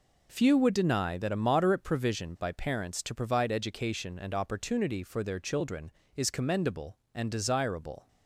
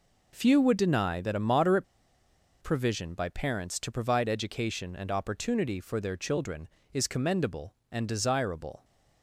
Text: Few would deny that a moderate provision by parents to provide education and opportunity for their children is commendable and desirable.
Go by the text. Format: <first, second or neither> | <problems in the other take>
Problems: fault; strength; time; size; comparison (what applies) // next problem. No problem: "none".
first | pauses between "moderate" and "provision"; noticeable; at 1.8 s; 0.77 s long